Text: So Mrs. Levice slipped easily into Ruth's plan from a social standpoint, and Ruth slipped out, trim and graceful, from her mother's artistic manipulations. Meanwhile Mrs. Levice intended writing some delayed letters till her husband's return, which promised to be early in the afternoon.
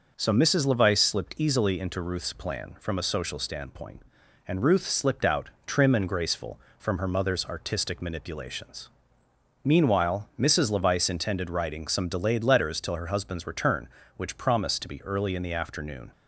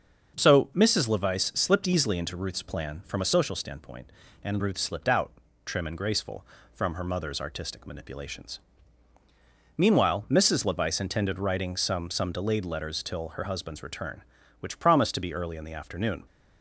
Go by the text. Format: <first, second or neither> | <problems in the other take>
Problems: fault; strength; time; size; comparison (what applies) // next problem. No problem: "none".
first | starts louder than the rest; until 1.4 s; 6.5 dB // says "some" twice; at 12.0 s